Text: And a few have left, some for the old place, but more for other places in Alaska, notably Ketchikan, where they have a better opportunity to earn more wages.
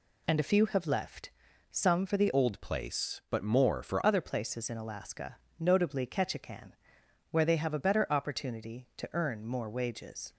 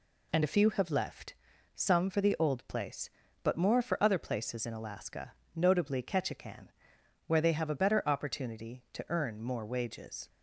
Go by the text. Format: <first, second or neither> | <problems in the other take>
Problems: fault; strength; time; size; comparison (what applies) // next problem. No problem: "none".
second | changes voice from "old" to "for"; from 2.3 to 4.0 s; 1.7 s long